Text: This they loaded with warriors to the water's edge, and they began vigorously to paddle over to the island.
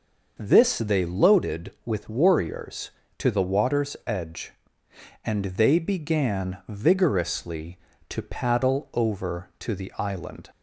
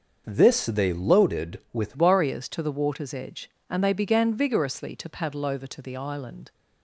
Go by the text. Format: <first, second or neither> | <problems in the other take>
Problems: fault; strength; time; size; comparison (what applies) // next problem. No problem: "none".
first | starts louder than the rest; until 1.2 s; 6.5 dB; noticeable in the first // changes voice at "warriors"; from 1.9 s on; 4.6 s long